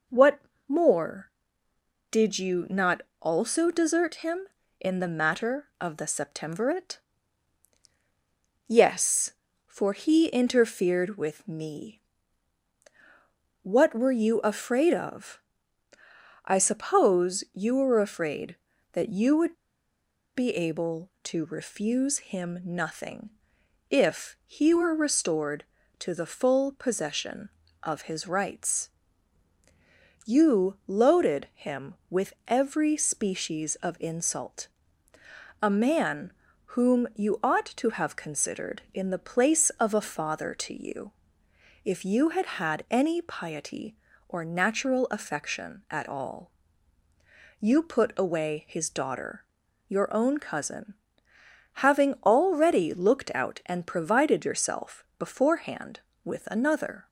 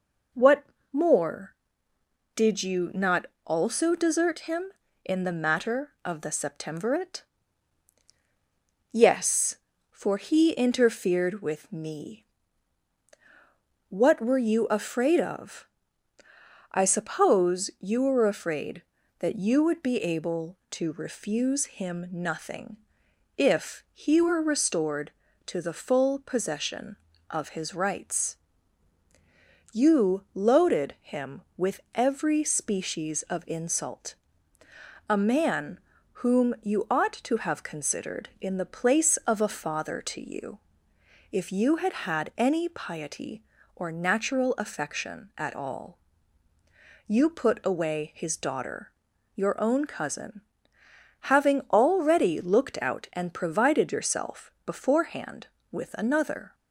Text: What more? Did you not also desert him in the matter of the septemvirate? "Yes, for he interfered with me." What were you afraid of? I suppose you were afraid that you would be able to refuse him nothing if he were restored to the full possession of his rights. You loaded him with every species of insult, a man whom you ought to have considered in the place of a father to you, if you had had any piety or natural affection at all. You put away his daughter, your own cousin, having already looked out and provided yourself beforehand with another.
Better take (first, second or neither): second